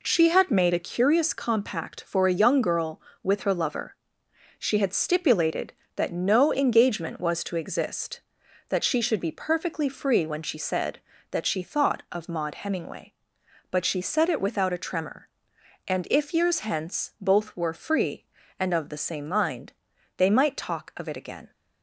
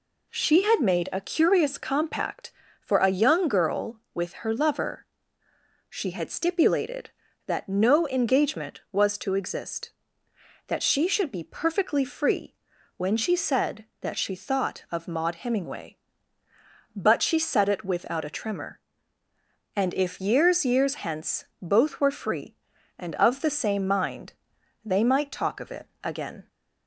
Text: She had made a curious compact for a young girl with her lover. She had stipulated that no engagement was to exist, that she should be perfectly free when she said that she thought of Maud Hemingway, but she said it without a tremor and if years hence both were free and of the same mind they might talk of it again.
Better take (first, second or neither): first